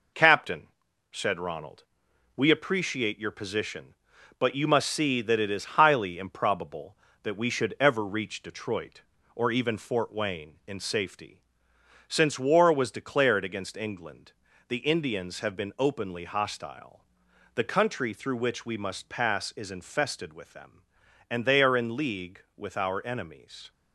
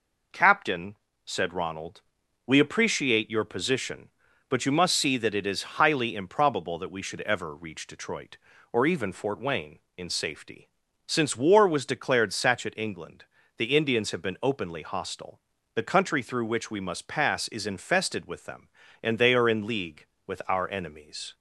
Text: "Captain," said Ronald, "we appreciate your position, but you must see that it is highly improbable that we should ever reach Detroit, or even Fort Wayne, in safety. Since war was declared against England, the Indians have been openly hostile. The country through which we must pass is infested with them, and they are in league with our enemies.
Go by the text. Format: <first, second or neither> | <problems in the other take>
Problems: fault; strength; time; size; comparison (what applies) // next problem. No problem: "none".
first | says "satchet" for "against"; at 12.3 s